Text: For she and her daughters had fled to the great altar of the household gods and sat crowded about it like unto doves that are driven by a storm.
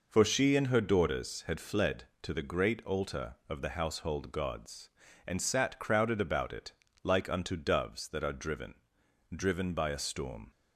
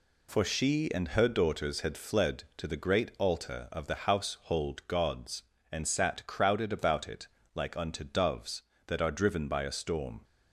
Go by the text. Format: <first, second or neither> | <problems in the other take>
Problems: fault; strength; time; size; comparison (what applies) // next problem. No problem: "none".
second | pauses between "it" and "like"; slight; at 6.7 s; 0.32 s long; slight in the second // says "driven" twice; at 9.3 s